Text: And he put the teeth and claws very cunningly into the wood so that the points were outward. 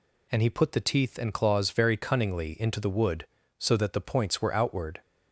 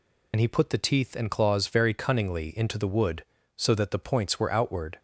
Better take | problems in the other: first | loses the start of "And"; at 0.3 s; 60 ms

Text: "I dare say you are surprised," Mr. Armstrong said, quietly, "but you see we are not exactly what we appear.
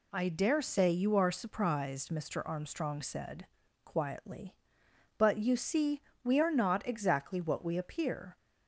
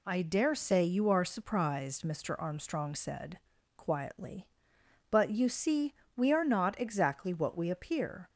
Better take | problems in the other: neither | pauses between "see" and "we"; slight; the same in both

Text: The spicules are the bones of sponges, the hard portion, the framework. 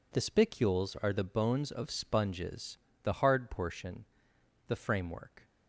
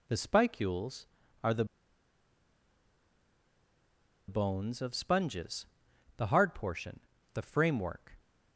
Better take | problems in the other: first | pauses between "the" and "bones"; strong; at 1.6 s; 2.6 s long

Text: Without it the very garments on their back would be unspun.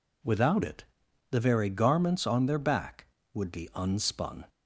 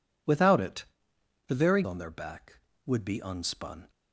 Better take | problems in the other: first | pauses between "it" and "the"; noticeable; at 0.8 s; 0.62 s long; noticeable in the first // skips "garments"; at 1.8 s

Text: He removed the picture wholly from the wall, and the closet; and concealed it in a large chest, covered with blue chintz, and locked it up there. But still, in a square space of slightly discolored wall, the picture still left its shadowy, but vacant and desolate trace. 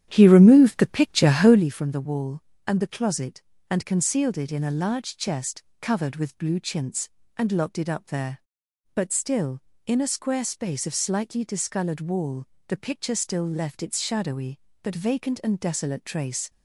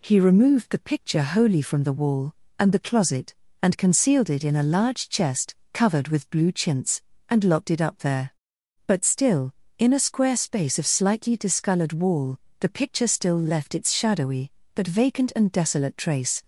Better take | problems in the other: second | starts louder than the rest; strong; until 1.7 s; 10.5 dB

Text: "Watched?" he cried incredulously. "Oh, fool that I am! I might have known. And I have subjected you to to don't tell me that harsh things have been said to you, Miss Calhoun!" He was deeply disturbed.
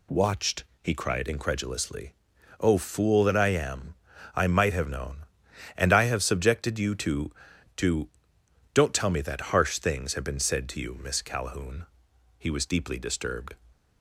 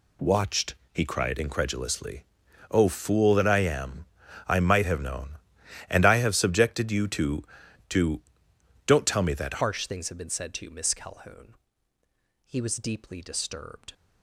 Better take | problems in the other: first | pauses between "to" and "don't"; noticeable; at 8.2 s; 0.64 s long; noticeable in the first // changes voice at "harsh"; from 9.6 s on; 4.3 s long

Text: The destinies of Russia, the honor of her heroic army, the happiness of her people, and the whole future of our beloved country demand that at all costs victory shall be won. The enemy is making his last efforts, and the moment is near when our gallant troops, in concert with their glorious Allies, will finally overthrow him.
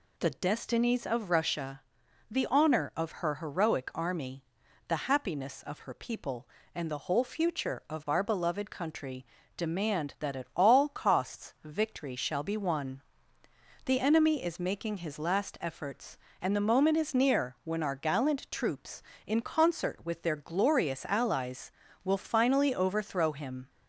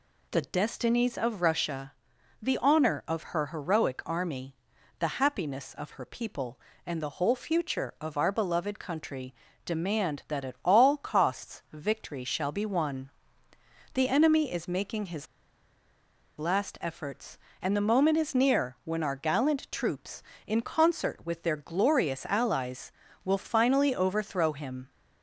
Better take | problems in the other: first | pauses between "country" and "demand"; slight; at 9.3 s; 0.30 s long; slight in the first // pauses between "his" and "last"; at 15.2 s; 1.1 s long

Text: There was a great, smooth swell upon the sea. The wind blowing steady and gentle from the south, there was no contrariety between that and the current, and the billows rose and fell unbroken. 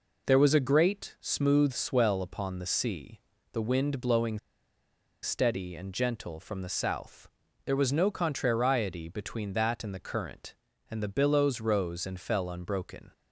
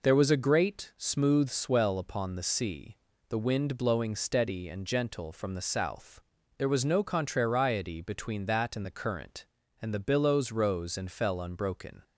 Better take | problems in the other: second | pauses between "blowing" and "steady"; noticeable; at 4.3 s; 0.84 s long

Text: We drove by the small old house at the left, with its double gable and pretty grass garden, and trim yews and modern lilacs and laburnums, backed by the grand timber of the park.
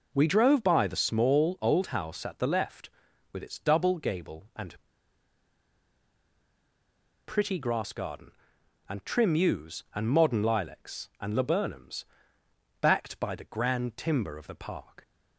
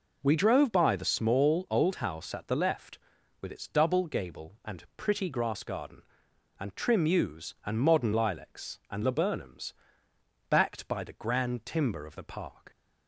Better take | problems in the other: second | pauses between "and" and "pretty"; strong; at 4.7 s; 2.5 s long

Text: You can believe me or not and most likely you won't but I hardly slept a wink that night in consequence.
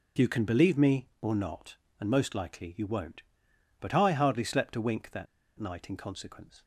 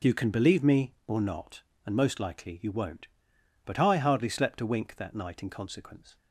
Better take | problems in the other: second | pauses between "that" and "night"; slight; at 5.2 s; 0.33 s long

